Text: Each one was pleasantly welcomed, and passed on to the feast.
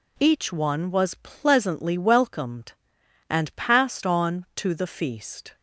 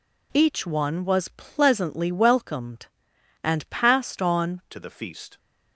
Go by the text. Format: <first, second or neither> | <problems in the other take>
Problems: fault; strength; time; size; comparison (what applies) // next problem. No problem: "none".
first | changes voice at "to"; from 4.7 s on; 0.6 s long